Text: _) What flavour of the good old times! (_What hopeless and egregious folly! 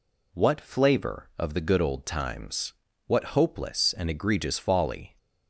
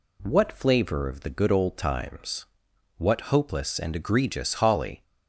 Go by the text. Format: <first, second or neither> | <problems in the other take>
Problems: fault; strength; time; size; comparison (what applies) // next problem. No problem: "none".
first | says "holly" for "folly"; at 4.5 s